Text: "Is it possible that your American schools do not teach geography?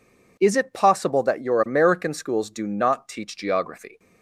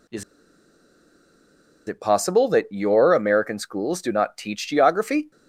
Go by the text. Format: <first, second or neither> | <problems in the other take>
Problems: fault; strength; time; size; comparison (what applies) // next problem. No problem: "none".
first | pauses between "Is" and "it"; strong; at 0.2 s; 1.6 s long